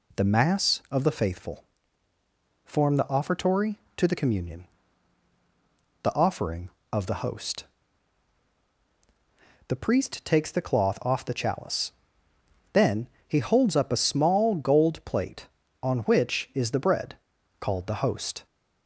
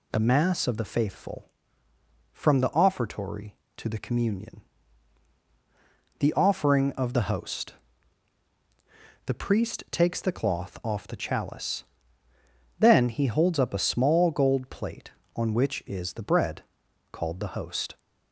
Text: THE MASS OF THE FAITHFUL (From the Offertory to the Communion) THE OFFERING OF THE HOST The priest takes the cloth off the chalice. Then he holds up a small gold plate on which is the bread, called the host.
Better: second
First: says "Form" for "From"; at 2.6 s // pauses between "HOST" and "The"; strong; at 7.6 s; 2.0 s long // pauses between "Then" and "he"; slight; at 13.0 s; 0.22 s long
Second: pauses between "HOST" and "The"; strong; at 7.7 s; 1.5 s long

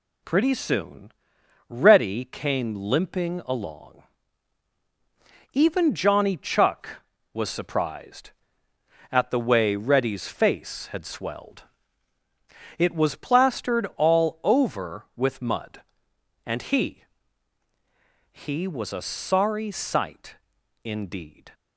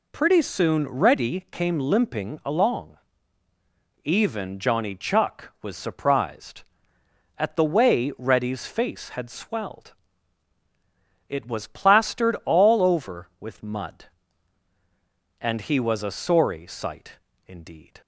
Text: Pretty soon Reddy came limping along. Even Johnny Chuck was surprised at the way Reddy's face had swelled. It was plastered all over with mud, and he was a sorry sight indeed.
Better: second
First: pauses between "soon" and "Reddy"; noticeable; at 1.1 s; 0.56 s long // says "he" twice; at 18.3 s // pauses between "sight" and "indeed"; noticeable; at 20.3 s; 0.48 s long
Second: pauses between "sight" and "indeed"; slight; at 17.1 s; 0.26 s long

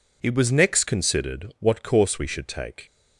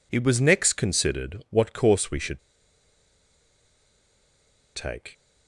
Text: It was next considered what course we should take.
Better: first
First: none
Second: pauses between "should" and "take"; strong; at 2.3 s; 2.3 s long

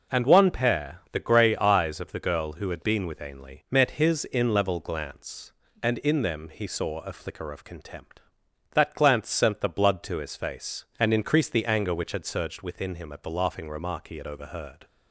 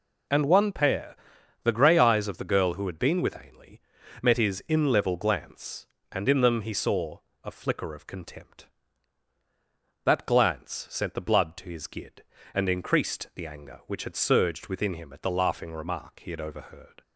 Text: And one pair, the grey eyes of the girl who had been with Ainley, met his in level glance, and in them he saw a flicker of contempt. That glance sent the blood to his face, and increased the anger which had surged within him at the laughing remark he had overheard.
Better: first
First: none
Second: pauses between "saw" and "a"; slight; at 7.1 s; 0.24 s long // says "gid" for "face"; at 11.8 s

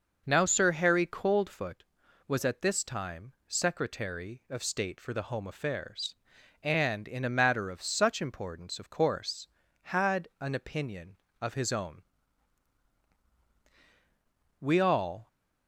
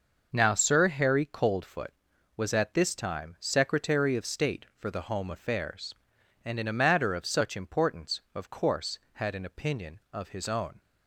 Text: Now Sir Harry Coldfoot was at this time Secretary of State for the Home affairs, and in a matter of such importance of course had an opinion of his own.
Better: second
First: goes on to say "We all"; noticeable; from 14.6 s on; 0.66 s long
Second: none

